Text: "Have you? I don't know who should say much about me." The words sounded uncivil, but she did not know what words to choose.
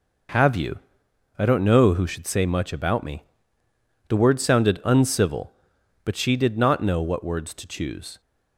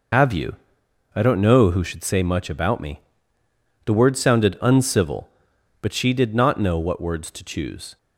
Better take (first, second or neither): first